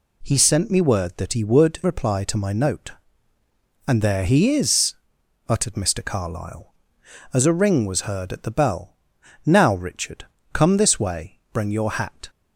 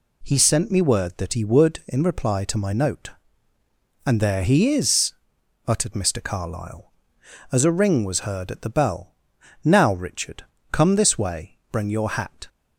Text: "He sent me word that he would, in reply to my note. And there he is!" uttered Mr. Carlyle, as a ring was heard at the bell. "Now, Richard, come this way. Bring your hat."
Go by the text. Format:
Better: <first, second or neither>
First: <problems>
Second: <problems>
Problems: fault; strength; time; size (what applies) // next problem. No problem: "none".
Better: second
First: skips "in"; at 1.8 s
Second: none